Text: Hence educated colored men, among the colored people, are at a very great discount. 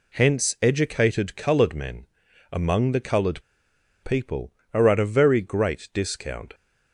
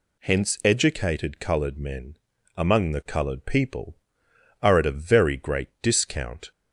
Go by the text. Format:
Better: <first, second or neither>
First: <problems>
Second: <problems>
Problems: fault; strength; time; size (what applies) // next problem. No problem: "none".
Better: second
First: pauses between "colored" and "people"; noticeable; at 3.4 s; 0.62 s long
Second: none